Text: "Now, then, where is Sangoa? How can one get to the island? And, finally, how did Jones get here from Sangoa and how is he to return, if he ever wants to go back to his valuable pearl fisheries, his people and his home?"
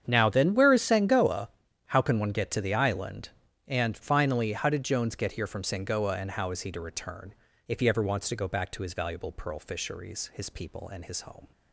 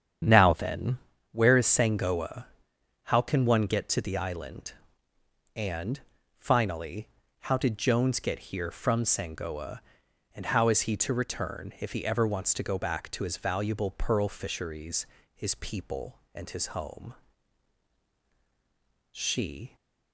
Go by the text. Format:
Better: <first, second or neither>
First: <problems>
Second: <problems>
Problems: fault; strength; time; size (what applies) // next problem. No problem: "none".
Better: first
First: starts louder than the rest; strong; until 1.0 s; 8.5 dB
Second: starts louder than the rest; strong; until 1.5 s; 8.5 dB // goes on to say "She"; noticeable; from 19.1 s on; 0.64 s long